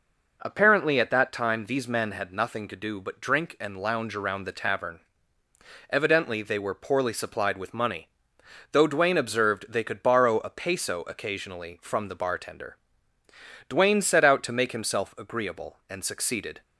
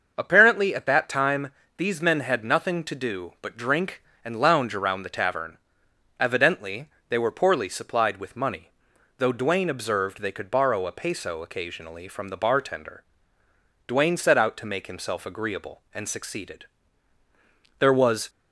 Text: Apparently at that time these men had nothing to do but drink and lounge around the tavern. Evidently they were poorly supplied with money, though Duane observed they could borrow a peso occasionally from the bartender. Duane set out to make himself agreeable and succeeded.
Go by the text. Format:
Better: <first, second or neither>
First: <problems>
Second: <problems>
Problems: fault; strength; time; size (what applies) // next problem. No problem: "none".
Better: first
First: none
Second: starts louder than the rest; until 1.1 s; 6.5 dB // pauses between "time" and "these"; slight; at 1.5 s; 0.26 s long // pauses between "Evidently" and "they"; slight; at 6.8 s; 0.20 s long // goes on to say "There was"; from 17.7 s on; 0.50 s long